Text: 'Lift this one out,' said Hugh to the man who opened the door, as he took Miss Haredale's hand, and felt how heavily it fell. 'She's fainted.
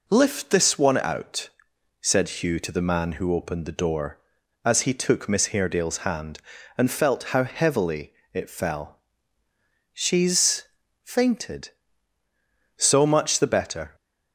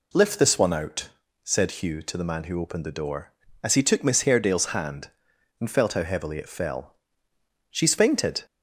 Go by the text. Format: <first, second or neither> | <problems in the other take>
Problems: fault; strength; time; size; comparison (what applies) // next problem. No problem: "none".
second | pauses between "heavily" and "it"; slight; at 8.1 s; 0.20 s long // pauses between "She's" and "fainted"; at 10.6 s; 0.40 s long // goes on to say "So much the better"; noticeable; from 12.7 s on; 1.1 s long